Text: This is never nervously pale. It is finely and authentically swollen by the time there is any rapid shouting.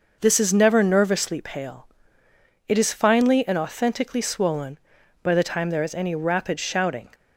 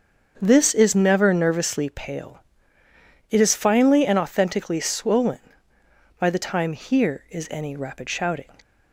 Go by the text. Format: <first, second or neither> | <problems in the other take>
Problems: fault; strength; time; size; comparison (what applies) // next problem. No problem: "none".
first | starts louder than the rest; until 1.4 s; 6.5 dB // says "here" for "there"; at 6.7 s